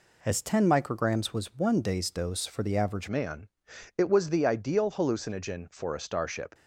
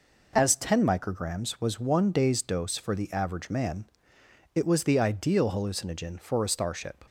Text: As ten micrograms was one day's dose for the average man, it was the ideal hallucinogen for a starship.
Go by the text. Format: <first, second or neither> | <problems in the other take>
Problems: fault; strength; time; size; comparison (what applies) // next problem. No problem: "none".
second | changes voice at "man"; from 3.0 s on; 3.5 s long